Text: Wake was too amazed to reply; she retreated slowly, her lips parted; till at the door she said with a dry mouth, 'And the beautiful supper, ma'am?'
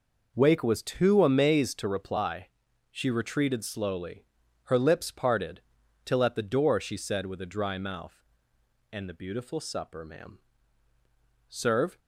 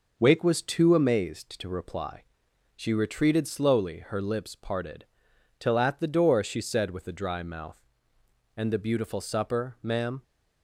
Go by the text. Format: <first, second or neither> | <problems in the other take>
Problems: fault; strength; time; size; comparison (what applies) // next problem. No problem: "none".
second | goes on to say "Serve"; slight; from 11.5 s on; 0.48 s long